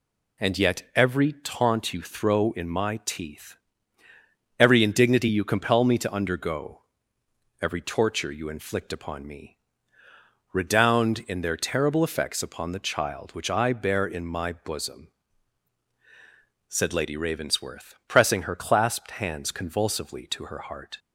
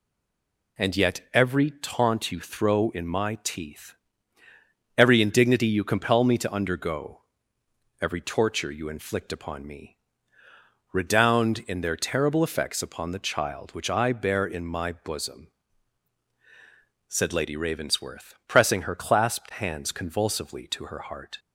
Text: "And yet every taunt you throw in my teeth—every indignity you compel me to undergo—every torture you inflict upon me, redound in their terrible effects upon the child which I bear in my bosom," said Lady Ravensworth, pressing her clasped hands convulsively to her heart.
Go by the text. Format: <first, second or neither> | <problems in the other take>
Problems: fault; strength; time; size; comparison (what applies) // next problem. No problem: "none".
first | stays silent before the first word; slight; until 0.7 s; 0.7 s long